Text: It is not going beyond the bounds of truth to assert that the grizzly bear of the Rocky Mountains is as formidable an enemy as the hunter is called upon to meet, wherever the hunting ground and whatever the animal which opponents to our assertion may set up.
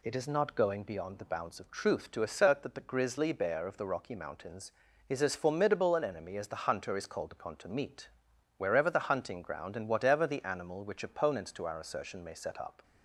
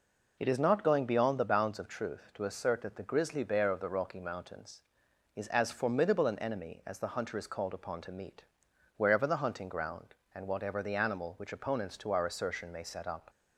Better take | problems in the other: neither | none

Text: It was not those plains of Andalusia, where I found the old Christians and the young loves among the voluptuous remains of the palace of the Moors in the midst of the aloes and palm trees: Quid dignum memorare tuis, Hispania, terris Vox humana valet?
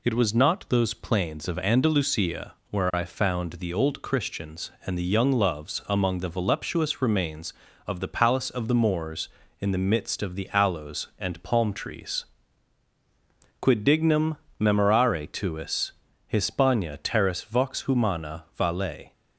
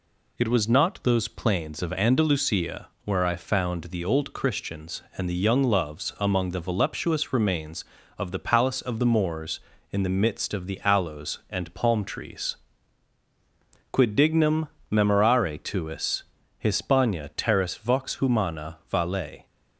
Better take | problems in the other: neither | pauses between "dignum" and "memorare"; slight; the same in both

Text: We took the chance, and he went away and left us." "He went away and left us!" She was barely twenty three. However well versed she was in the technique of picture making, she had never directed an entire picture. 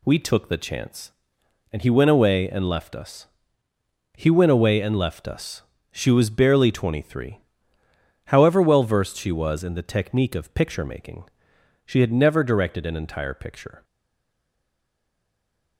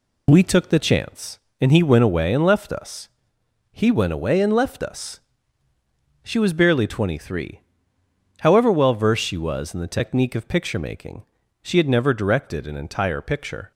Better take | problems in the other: second | stays silent after the last word; noticeable; from 13.8 s on; 1.9 s long

